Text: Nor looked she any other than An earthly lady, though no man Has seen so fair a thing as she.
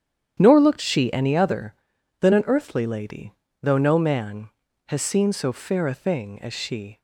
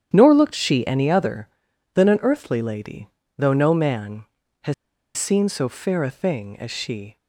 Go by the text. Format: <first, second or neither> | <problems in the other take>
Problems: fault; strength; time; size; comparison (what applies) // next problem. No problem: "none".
first | starts louder than the rest; strong; until 1.1 s; 9.5 dB; strong in the first // pauses between "Has" and "seen"; at 4.7 s; 0.42 s long